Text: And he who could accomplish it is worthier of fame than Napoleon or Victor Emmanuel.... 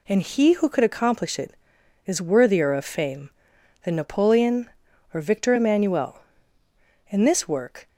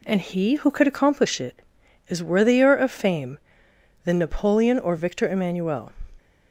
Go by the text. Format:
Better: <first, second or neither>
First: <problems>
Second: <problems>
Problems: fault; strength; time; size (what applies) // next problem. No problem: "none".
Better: second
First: goes on to say "In this work"; noticeable; from 7.0 s on; 0.79 s long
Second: none